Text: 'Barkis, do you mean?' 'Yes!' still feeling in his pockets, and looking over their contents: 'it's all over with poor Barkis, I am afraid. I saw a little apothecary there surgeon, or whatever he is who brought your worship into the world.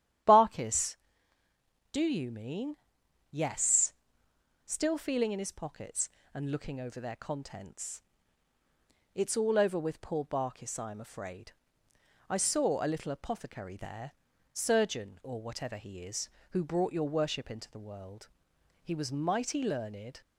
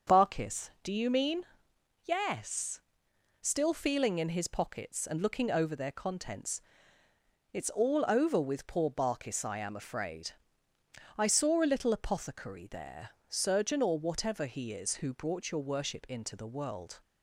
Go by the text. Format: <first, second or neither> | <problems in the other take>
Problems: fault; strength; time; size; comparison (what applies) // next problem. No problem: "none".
second | starts louder than the rest; strong; until 2.2 s; 11 dB; also in the second // pauses between "there" and "surgeon"; at 14.1 s; 0.40 s long; slight in the second // goes on to say "He was mighty learned"; from 18.8 s on; 1.3 s long